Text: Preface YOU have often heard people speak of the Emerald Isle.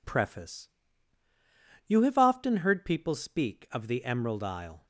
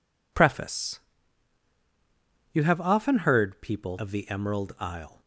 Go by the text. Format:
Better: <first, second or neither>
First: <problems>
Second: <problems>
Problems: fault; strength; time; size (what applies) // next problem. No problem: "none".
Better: first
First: pauses between "Preface" and "YOU"; at 0.6 s; 1.1 s long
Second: pauses between "Preface" and "YOU"; strong; at 0.9 s; 1.5 s long // skips "speak"; at 3.9 s